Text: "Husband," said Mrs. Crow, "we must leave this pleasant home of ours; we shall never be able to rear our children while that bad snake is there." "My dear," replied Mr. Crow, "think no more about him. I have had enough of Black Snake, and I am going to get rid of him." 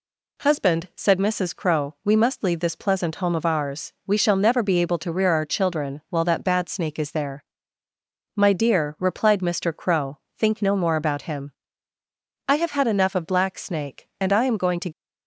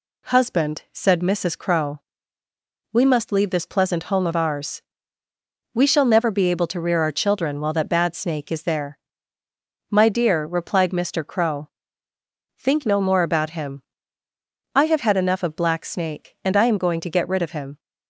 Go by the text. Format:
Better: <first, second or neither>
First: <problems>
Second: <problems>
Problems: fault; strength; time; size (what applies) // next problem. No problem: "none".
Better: second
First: stops before "get rid of him"; at 14.9 s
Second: none